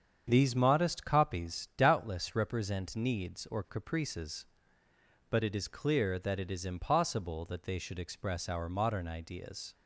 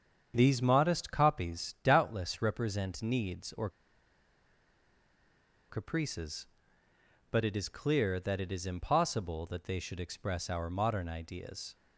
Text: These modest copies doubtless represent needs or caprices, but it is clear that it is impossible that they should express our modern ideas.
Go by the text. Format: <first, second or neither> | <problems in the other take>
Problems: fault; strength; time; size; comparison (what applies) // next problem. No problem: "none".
first | starts louder than the rest; strong; until 1.3 s; 7.5 dB; strong in the first // pauses between "or" and "caprices"; strong; at 3.6 s; 2.0 s long